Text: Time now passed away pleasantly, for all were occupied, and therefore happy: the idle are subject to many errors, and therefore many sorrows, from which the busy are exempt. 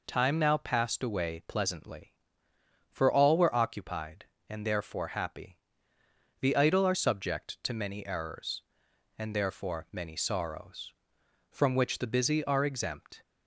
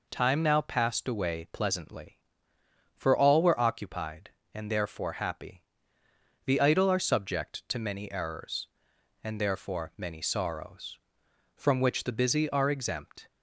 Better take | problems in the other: neither | none

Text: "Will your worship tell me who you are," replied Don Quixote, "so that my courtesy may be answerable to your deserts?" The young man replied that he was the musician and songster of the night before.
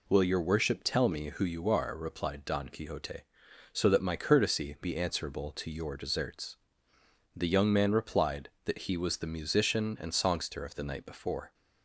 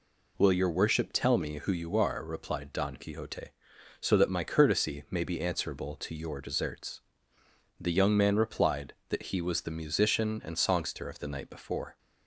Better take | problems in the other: second | skips "may"; at 4.7 s

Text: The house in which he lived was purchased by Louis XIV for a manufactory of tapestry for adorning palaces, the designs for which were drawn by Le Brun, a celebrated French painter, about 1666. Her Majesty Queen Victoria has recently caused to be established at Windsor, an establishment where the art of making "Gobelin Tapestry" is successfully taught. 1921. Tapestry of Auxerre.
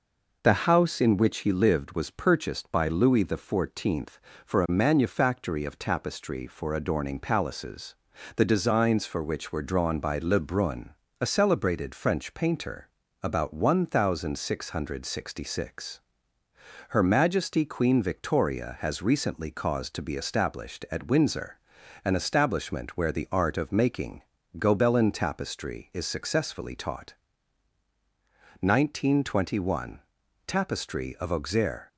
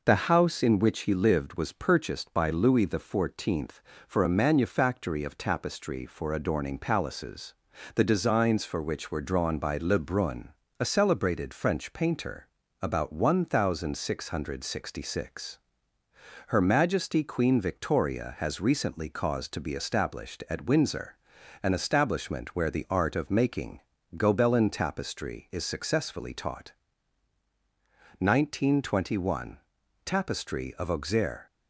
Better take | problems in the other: neither | pauses between "making" and "Gobelin"; slight; the same in both

